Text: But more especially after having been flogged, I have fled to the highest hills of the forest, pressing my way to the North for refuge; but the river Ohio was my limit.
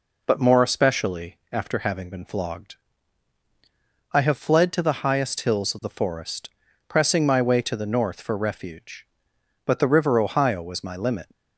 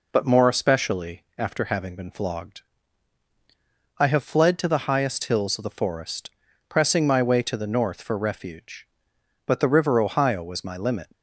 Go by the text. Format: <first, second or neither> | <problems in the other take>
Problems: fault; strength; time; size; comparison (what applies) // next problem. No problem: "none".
neither | none